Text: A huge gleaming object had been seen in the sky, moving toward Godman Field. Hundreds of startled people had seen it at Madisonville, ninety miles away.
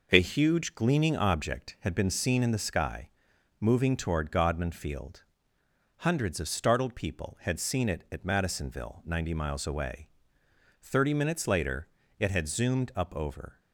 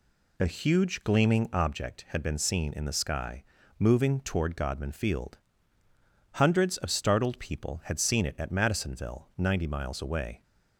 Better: second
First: goes on to say "Thirty minutes later it had zoomed up over"; strong; from 10.8 s on; 2.7 s long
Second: none

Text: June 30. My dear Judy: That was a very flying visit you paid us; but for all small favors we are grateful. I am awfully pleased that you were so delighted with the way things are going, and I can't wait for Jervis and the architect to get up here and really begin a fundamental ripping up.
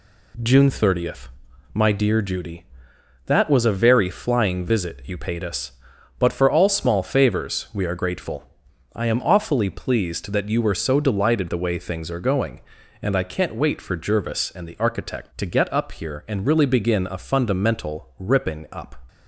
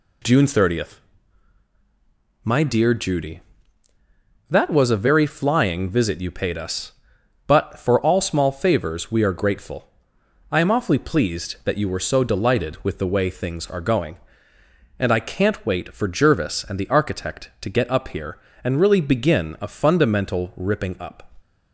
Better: second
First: skips "with"; at 11.4 s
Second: none

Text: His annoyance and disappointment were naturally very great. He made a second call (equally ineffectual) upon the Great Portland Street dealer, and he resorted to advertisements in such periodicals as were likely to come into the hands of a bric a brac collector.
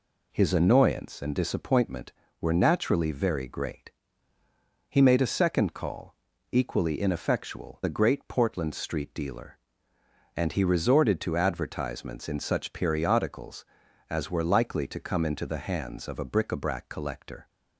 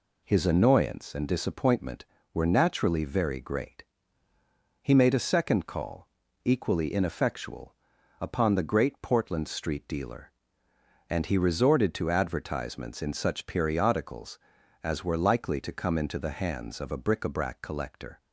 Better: second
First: skips "upon"; at 7.8 s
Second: none

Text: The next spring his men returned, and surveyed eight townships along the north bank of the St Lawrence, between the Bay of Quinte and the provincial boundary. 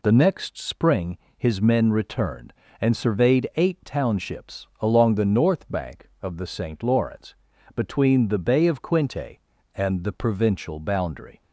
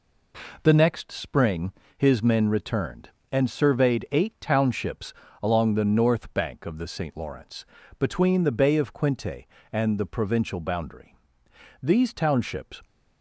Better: first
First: pauses between "spring" and "his"; slight; at 1.1 s; 0.18 s long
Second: pauses between "spring" and "his"; slight; at 1.7 s; 0.24 s long // pauses between "townships" and "along"; slight; at 5.1 s; 0.28 s long // goes on to say "These townships"; noticeable; from 11.8 s on; 1.0 s long

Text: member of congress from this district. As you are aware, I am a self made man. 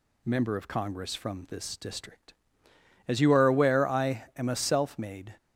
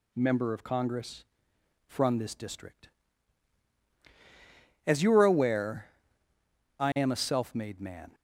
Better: second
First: stops before "man"; at 5.3 s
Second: none

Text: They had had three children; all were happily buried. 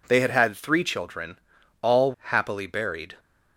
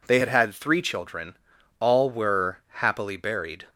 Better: second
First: skips "were"; at 2.1 s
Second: none

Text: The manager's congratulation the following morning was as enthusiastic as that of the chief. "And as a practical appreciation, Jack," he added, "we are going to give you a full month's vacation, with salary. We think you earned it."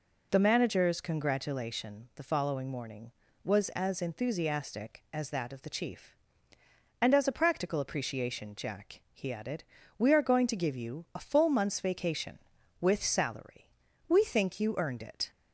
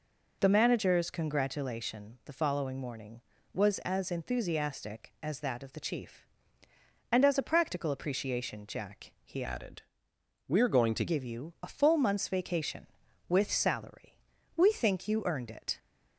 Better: first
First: none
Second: changes voice from "added" to "to"; from 9.4 to 11.0 s; 1.6 s long

